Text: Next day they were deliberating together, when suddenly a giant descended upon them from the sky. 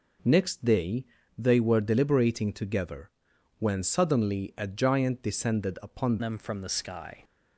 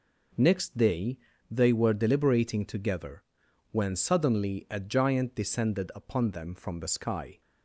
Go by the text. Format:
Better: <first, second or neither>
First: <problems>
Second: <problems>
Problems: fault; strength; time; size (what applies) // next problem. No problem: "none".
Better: second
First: pauses between "day" and "they"; slight; at 1.0 s; 0.32 s long // changes voice at "them"; from 6.1 s on; 1.1 s long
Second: pauses between "day" and "they"; slight; at 1.1 s; 0.32 s long